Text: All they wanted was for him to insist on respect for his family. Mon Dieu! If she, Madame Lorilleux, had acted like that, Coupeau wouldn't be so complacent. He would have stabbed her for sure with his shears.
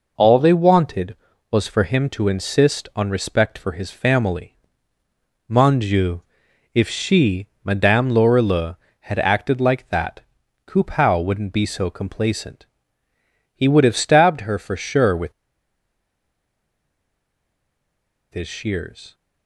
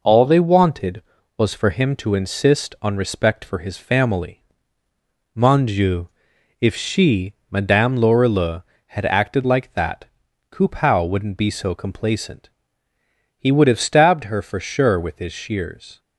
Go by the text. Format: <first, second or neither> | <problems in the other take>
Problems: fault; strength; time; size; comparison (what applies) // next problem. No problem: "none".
second | pauses between "with" and "his"; strong; at 15.3 s; 3.0 s long